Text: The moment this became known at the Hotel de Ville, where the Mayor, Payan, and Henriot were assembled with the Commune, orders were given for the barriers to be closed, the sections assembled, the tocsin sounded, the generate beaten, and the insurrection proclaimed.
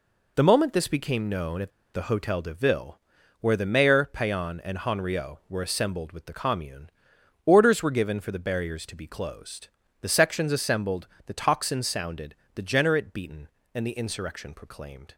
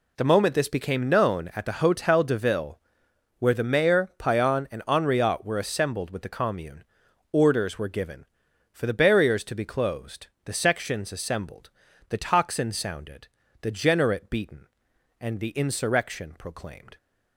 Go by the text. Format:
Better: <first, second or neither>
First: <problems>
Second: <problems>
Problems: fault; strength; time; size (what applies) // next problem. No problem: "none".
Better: second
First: pauses between "at" and "the"; slight; at 1.7 s; 0.23 s long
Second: none